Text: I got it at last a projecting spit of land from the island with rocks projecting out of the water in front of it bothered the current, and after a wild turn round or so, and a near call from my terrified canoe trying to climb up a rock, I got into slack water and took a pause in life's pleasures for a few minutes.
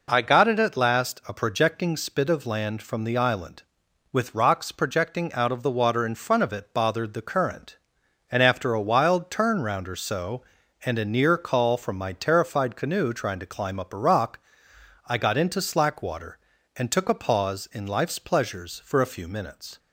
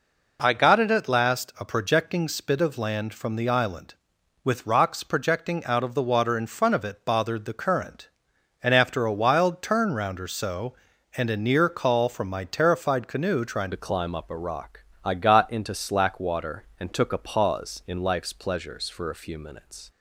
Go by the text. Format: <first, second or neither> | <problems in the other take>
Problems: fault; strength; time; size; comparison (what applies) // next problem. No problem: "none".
first | changes voice at "to"; from 13.7 s on; 6.1 s long